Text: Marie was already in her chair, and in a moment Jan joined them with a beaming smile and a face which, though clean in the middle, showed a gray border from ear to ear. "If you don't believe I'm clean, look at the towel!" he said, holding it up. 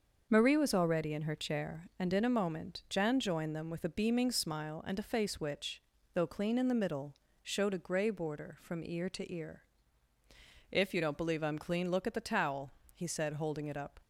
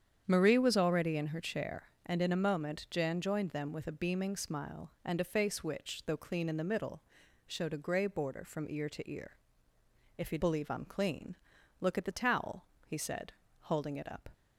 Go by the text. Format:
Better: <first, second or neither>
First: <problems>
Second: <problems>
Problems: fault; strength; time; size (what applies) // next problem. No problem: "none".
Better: first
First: starts louder than the rest; until 1.3 s; 6 dB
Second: starts louder than the rest; strong; until 1.2 s; 8.5 dB // skips "don't"; at 10.3 s